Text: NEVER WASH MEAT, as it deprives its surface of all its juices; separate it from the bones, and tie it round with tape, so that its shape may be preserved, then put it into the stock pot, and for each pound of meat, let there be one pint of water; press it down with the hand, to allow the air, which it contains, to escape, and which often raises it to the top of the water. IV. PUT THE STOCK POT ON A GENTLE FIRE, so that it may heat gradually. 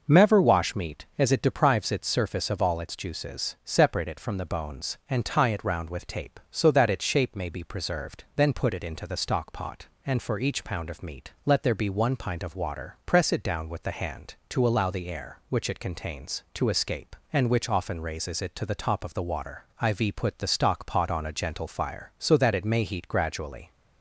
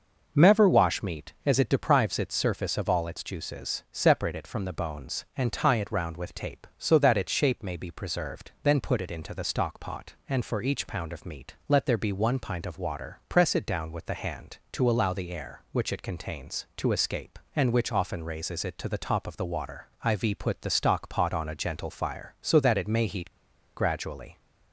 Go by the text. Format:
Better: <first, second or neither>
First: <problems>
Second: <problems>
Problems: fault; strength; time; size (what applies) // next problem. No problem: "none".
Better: first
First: none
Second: pauses between "heat" and "gradually"; at 23.3 s; 0.44 s long